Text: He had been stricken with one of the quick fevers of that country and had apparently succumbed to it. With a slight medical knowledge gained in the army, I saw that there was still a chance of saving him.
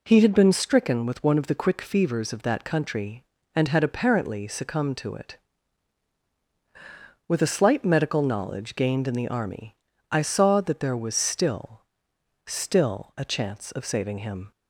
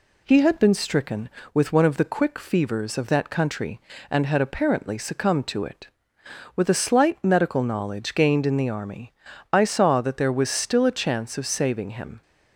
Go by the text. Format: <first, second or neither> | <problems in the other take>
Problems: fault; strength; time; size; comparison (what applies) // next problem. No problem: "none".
second | says "still" twice; at 12.4 s